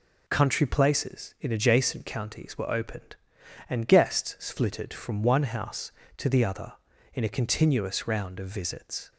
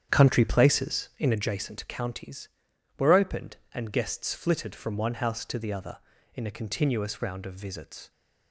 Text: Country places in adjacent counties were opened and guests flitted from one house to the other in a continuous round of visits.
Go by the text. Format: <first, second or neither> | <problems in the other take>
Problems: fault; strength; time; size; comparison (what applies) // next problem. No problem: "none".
first | starts louder than the rest; strong; until 1.5 s; 9 dB